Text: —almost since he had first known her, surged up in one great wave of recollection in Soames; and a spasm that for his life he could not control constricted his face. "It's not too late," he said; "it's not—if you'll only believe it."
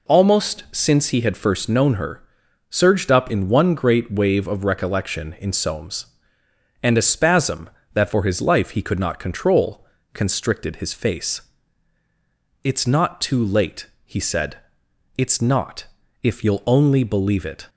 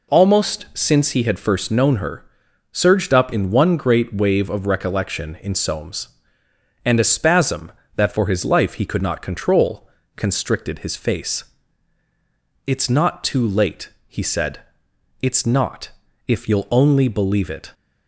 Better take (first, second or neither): neither